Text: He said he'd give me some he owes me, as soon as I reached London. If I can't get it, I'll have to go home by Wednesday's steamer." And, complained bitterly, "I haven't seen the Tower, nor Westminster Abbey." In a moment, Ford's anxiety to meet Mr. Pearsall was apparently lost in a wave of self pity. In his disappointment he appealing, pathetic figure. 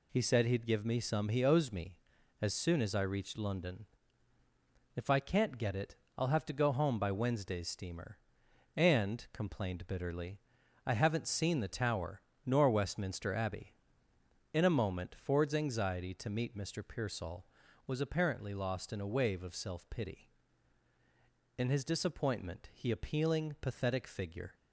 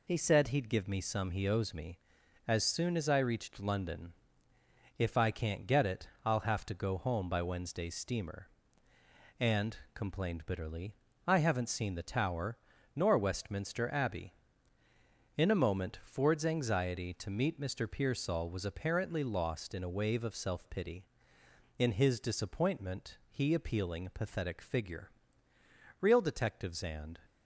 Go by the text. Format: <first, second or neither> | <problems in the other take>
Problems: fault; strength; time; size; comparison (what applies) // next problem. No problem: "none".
first | goes on to say "Real detectives and"; noticeable; from 25.9 s on; 1.1 s long